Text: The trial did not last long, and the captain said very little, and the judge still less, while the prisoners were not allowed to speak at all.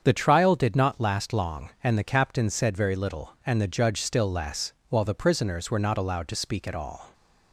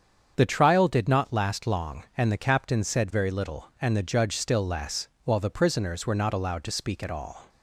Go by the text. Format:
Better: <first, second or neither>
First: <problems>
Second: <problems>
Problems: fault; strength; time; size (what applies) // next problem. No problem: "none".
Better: neither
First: starts louder than the rest; strong; until 1.0 s; 7.5 dB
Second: starts louder than the rest; strong; until 1.3 s; 7.5 dB